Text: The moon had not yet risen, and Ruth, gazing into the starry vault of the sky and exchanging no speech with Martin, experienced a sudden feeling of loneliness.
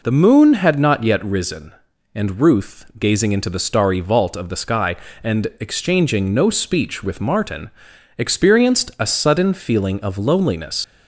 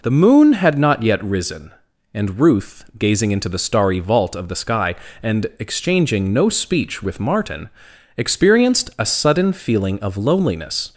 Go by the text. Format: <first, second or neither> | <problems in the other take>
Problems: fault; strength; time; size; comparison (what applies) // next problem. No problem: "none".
second | leaves "loneliness" unfinished; at 10.8 s; 95 ms